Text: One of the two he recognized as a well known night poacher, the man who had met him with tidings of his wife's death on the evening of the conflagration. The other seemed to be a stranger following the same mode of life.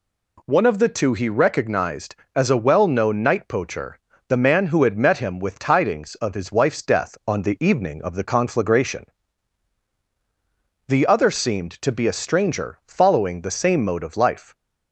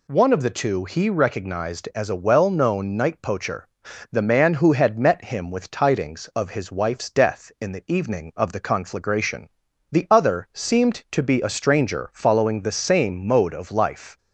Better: first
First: none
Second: says "in" for "on"; at 7.6 s

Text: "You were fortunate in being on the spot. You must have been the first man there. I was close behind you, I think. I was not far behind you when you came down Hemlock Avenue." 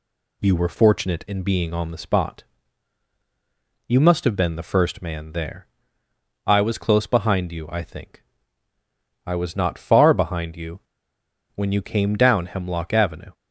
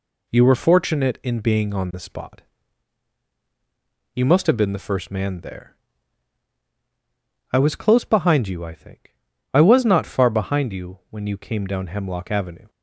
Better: second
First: pauses between "you" and "when"; noticeable; at 10.7 s; 0.75 s long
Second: none

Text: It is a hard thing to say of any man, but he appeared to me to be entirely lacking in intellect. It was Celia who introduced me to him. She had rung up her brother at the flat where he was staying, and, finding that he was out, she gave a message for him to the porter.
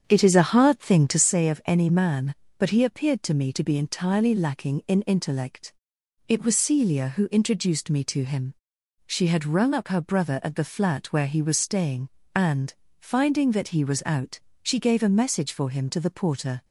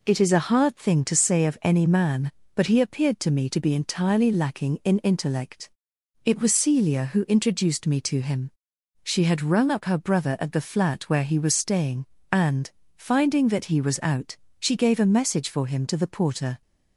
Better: second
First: starts louder than the rest; strong; until 1.3 s; 7.5 dB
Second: none

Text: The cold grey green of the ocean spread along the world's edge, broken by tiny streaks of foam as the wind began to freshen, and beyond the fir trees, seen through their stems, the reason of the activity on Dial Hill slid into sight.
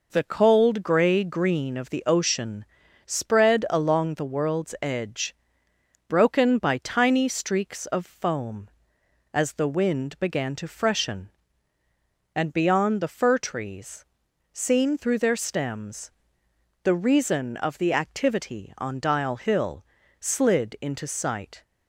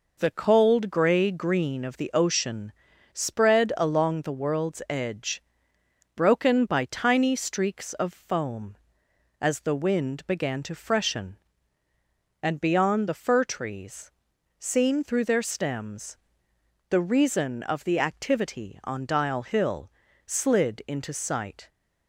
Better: neither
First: pauses between "ocean" and "spread"; at 2.6 s; 0.40 s long // pauses between "Hill" and "slid"; slight; at 19.8 s; 0.34 s long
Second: pauses between "ocean" and "spread"; at 2.7 s; 0.40 s long // pauses between "Hill" and "slid"; slight; at 19.9 s; 0.34 s long

